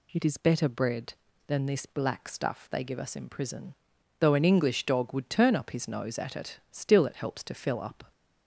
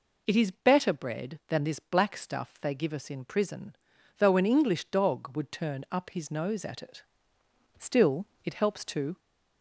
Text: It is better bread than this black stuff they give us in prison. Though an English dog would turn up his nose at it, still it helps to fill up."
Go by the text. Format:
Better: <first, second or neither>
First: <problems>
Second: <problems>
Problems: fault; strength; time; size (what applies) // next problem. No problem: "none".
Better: first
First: none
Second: pauses between "still" and "it"; slight; at 8.2 s; 0.18 s long // stops before "fill up"; at 9.1 s